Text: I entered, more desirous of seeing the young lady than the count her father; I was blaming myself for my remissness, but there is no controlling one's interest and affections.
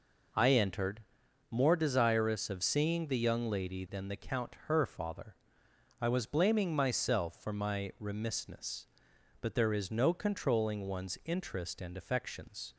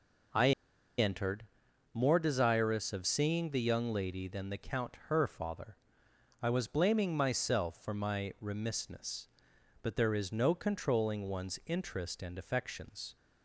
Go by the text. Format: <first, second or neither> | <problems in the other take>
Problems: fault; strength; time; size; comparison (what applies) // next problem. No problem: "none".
first | pauses between "I" and "entered"; noticeable; at 0.5 s; 0.47 s long